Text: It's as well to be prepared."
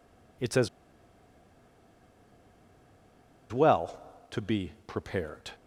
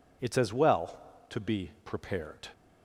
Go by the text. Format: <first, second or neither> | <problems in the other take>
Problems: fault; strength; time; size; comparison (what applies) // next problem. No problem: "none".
second | pauses between "as" and "well"; strong; at 0.6 s; 2.8 s long